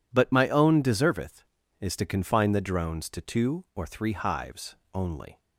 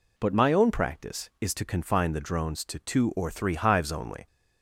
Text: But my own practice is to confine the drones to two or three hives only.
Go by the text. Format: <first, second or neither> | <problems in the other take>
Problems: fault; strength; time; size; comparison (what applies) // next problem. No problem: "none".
second | says "deserveth" for "practice"; at 0.8 s // pauses between "hives" and "only"; slight; at 4.7 s; 0.18 s long